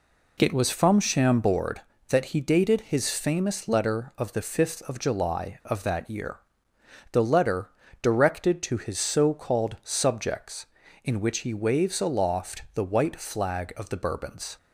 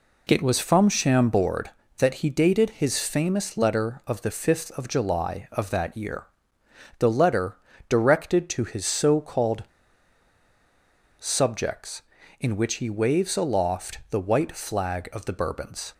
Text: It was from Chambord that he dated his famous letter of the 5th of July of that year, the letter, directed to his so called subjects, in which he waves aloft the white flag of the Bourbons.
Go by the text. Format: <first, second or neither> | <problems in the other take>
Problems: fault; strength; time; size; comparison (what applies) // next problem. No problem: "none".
first | pauses between "called" and "subjects"; strong; at 9.6 s; 1.5 s long